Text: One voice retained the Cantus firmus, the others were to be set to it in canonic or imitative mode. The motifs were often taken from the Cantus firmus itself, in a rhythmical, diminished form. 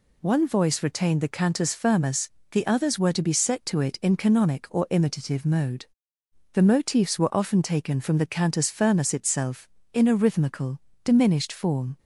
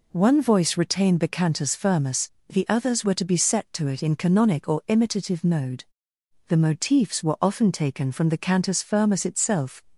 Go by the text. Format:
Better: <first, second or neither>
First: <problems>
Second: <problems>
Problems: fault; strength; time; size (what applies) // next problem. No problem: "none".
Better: first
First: none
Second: stops before "in a rhythmical diminished form"; at 9.9 s